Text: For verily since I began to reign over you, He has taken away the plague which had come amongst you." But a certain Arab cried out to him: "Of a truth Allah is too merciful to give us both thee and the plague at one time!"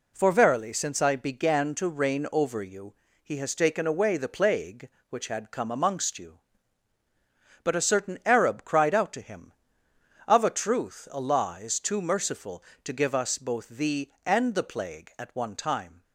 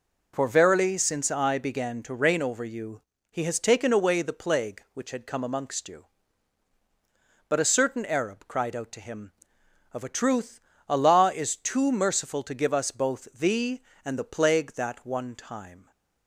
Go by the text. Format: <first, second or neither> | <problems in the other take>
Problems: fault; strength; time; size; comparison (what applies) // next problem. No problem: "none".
first | pauses between "truth" and "Allah"; slight; at 10.5 s; 0.30 s long // says "that" for "at"; at 14.7 s